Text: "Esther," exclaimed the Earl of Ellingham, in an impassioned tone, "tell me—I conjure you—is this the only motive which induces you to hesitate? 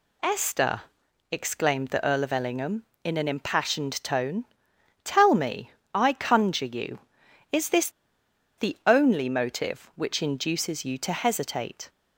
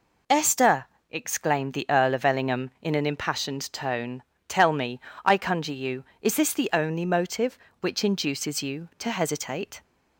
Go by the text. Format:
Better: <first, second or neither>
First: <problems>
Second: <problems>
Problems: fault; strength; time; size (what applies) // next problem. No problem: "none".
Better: second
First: pauses between "this" and "the"; noticeable; at 7.8 s; 0.68 s long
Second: none